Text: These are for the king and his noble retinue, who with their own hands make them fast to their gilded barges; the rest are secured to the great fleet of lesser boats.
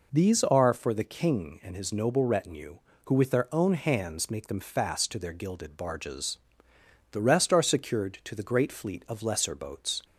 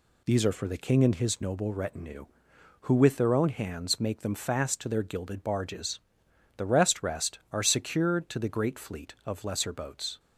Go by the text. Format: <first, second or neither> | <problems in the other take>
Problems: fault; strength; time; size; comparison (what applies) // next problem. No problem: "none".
first | says "rest" twice; at 7.0 s